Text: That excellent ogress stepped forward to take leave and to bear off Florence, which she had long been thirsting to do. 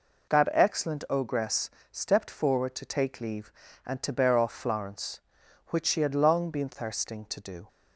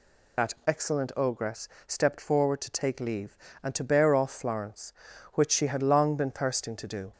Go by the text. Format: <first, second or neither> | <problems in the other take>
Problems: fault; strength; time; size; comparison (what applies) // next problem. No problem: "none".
first | loses the start of "That"; at 0.3 s; 40 ms // pauses between "ogress" and "stepped"; slight; at 1.6 s; 0.16 s long; slight in the first